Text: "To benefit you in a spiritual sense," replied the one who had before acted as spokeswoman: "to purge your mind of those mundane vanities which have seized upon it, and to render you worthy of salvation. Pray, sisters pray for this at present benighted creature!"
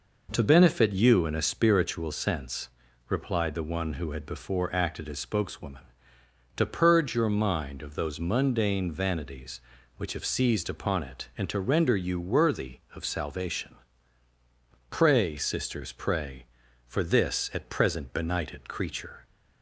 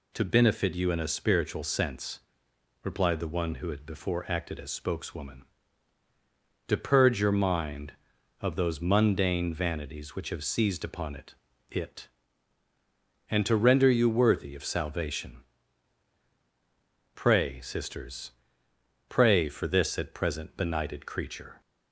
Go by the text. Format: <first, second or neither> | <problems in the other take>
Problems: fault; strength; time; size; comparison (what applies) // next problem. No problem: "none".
first | says "it" twice; at 11.7 s // pauses between "sisters" and "pray"; noticeable; at 18.3 s; 0.76 s long